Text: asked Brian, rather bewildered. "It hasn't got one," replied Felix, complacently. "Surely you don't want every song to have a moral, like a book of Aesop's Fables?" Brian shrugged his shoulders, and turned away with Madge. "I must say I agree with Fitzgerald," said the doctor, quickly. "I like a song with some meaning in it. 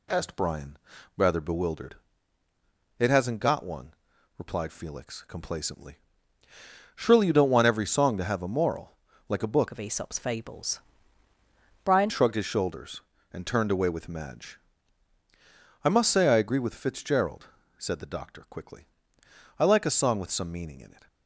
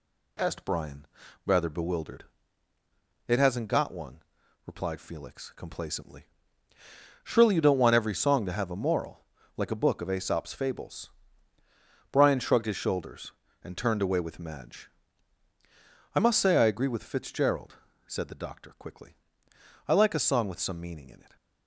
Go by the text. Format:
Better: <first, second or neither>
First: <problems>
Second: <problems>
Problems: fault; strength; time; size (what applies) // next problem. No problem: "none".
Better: second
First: changes voice from "of" to "Brian"; from 9.7 to 12.1 s; 2.4 s long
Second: none